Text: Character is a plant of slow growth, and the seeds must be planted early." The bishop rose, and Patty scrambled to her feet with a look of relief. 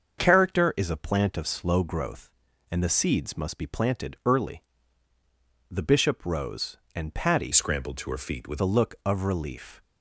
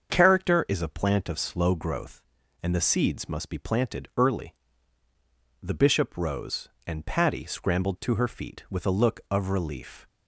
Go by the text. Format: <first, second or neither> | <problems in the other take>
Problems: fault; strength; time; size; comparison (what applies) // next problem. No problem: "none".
second | starts louder than the rest; until 1.2 s; 6.5 dB; also in the second // changes voice from "scrambled" to "with"; from 7.5 to 8.6 s; 1.1 s long